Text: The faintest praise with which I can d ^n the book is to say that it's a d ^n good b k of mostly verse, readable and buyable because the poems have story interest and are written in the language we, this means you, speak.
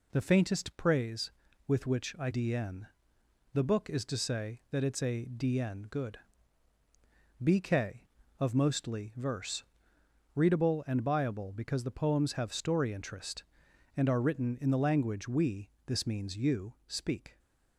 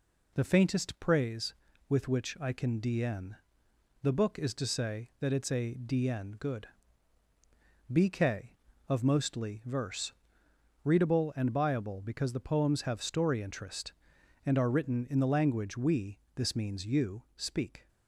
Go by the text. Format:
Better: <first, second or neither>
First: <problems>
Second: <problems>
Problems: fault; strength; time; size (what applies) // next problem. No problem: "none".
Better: second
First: skips "can"; at 2.3 s // pauses between "n" and "the"; noticeable; at 2.8 s; 0.68 s long // pauses between "good" and "b"; at 6.1 s; 1.2 s long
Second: pauses between "n" and "the"; noticeable; at 3.3 s; 0.68 s long // pauses between "good" and "b"; at 6.6 s; 1.2 s long